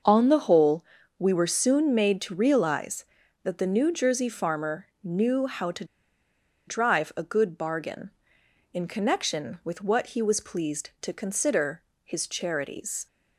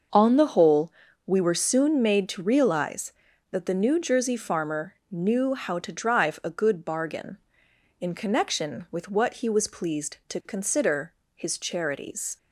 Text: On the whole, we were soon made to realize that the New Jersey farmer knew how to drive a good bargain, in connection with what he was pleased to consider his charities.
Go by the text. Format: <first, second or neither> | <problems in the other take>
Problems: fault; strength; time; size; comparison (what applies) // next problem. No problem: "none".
second | starts louder than the rest; until 1.4 s; 6.5 dB; also in the second // pauses between "farmer" and "knew"; slight; at 4.8 s; 0.16 s long; slight in the second // pauses between "to" and "drive"; noticeable; at 5.8 s; 0.83 s long // pauses between "consider" and "his"; slight; at 11.8 s; 0.22 s long; slight in the second